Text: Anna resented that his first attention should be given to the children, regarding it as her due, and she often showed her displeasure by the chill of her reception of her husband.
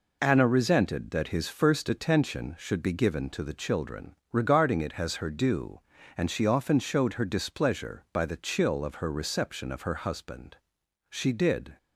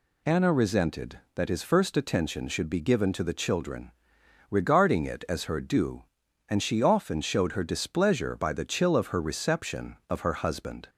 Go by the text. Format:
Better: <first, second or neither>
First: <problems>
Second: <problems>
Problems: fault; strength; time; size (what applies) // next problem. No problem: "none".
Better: second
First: goes on to say "She did"; noticeable; from 11.1 s on; 0.66 s long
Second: none